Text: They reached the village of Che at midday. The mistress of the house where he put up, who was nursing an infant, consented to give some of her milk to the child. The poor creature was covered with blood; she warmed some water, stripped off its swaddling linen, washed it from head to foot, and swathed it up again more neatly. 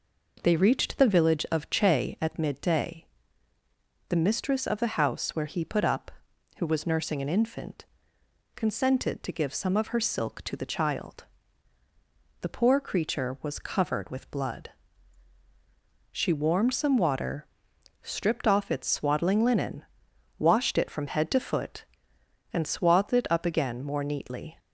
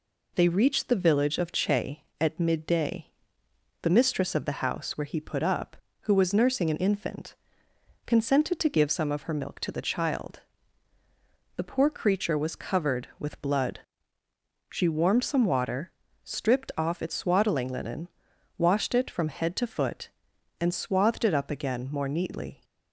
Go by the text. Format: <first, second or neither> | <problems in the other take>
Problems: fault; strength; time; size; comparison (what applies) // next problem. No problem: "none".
second | says "silk" for "milk"; at 10.0 s